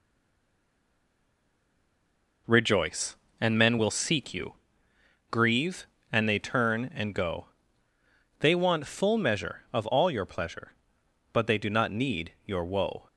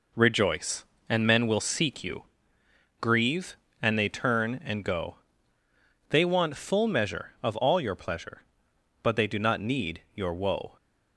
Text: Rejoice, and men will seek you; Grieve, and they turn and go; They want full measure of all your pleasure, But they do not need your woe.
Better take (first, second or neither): second